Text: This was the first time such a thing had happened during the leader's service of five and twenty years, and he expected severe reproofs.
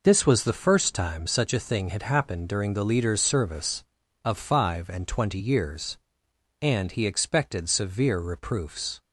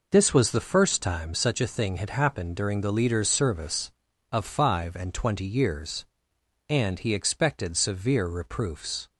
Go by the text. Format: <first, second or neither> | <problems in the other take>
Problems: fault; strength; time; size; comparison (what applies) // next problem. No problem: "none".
neither | none